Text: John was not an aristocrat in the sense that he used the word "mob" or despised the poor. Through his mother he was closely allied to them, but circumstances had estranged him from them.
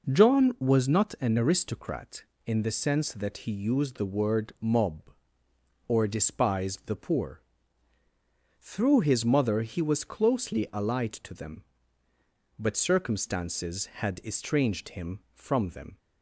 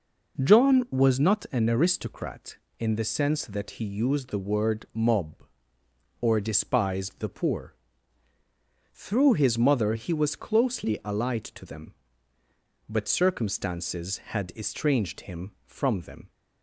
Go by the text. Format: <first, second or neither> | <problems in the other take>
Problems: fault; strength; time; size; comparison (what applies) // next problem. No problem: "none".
neither | none